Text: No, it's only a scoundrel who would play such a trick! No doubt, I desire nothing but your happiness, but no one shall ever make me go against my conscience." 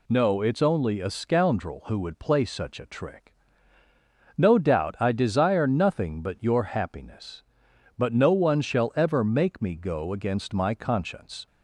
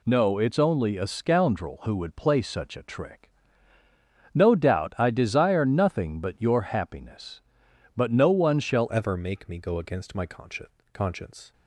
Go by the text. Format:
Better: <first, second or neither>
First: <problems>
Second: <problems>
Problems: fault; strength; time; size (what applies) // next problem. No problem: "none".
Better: first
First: none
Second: changes voice at "ever"; from 8.9 s on; 2.6 s long